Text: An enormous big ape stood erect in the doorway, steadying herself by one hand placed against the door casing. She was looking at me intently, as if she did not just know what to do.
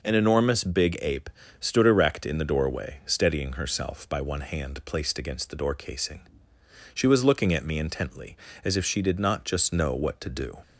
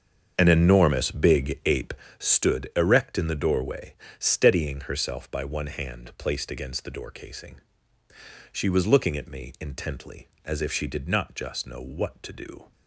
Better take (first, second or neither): first